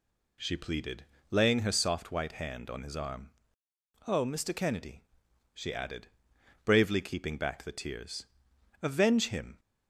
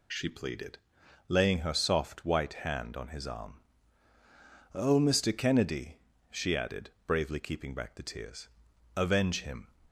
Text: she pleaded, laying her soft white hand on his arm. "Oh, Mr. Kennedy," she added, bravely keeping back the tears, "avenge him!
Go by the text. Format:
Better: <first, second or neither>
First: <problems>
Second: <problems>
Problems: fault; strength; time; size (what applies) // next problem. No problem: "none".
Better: neither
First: none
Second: none